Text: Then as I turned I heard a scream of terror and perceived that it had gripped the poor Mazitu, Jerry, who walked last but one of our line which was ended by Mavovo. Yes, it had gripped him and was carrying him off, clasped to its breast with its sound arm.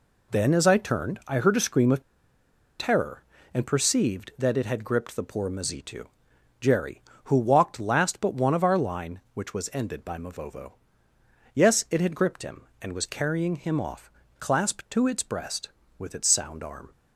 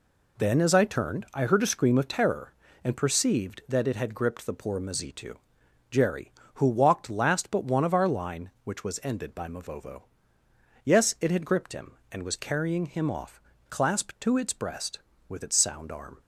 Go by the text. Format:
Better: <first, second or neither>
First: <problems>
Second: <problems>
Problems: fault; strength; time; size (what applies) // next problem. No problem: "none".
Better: second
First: pauses between "of" and "terror"; noticeable; at 2.0 s; 0.77 s long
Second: none